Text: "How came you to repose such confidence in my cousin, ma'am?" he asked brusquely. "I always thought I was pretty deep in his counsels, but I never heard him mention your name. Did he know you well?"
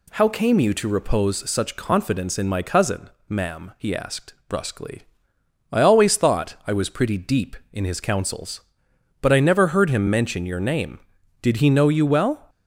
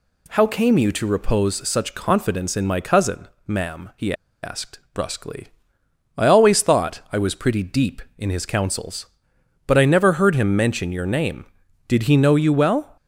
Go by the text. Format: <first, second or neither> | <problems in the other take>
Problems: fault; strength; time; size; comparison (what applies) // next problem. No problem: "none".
first | pauses between "he" and "asked"; slight; at 4.1 s; 0.30 s long // pauses between "asked" and "brusquely"; slight; at 4.7 s; 0.16 s long; slight in the first